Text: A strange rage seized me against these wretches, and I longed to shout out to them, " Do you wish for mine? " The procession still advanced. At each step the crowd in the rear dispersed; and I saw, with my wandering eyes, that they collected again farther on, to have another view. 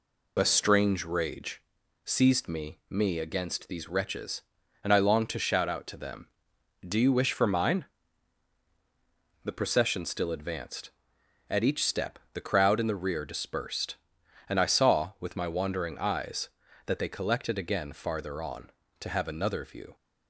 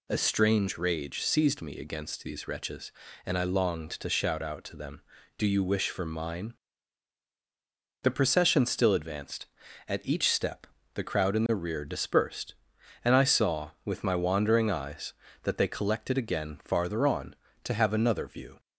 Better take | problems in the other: second | pauses between "rage" and "seized"; at 1.6 s; 0.40 s long // says "me" twice; at 2.8 s // pauses between "step" and "the"; slight; at 12.1 s; 0.16 s long; slight in the second

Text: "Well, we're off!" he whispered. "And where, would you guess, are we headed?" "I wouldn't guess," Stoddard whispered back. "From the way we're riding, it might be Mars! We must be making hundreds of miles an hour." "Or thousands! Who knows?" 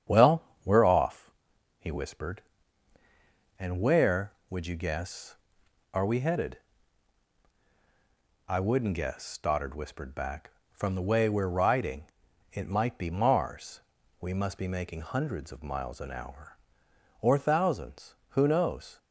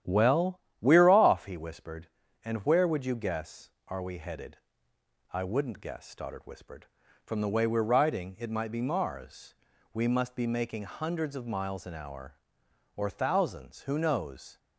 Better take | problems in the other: first | starts louder than the rest; strong; until 1.2 s; 10.5 dB; strong in the first // skips "back"; at 7.0 s

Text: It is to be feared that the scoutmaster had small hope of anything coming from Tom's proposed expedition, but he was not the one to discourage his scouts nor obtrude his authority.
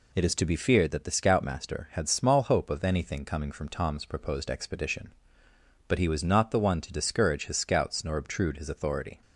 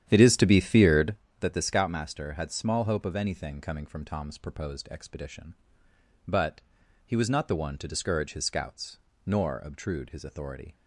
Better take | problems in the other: first | starts louder than the rest; strong; until 1.2 s; 10 dB // pauses between "but" and "he"; at 6.6 s; 0.44 s long // pauses between "scouts" and "nor"; slight; at 8.9 s; 0.28 s long

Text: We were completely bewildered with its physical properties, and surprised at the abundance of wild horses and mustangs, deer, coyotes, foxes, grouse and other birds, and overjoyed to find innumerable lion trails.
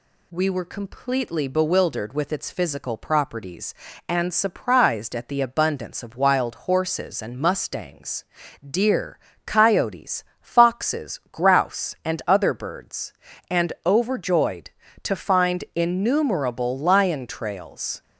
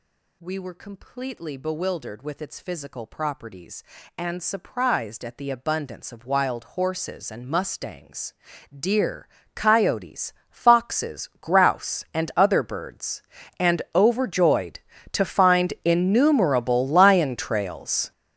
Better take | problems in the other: first | gets louder; strong; throughout; 16.5 dB

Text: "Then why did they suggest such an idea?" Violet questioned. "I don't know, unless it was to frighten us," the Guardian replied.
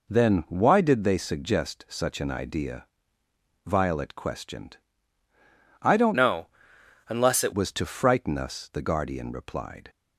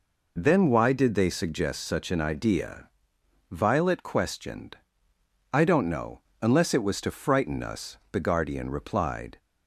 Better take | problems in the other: second | changes voice from "know" to "it"; from 6.1 to 7.5 s; 1.4 s long

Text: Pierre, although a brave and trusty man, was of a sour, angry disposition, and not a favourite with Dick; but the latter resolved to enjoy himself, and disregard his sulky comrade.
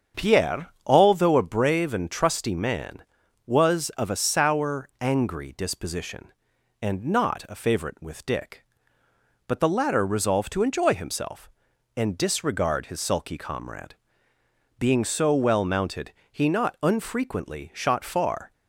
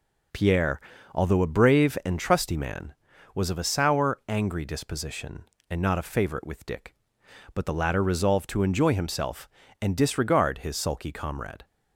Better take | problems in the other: second | starts louder than the rest; strong; until 1.3 s; 7.5 dB // goes on to say "Being so well mounted he not unfrequently shot far"; strong; from 14.7 s on; 3.7 s long

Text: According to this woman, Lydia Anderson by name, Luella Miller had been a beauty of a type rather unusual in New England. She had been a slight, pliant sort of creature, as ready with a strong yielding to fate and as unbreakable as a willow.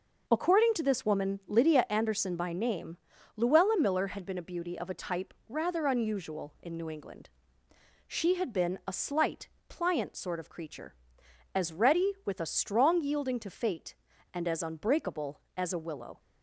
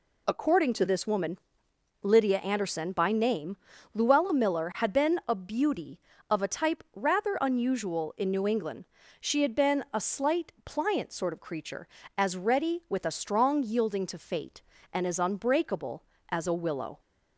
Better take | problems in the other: neither | none

